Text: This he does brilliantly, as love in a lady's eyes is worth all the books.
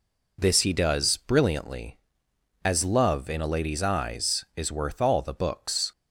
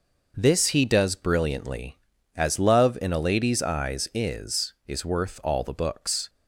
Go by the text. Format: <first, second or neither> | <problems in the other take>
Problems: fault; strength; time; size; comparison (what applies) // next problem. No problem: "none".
first | says "is" twice; at 4.8 s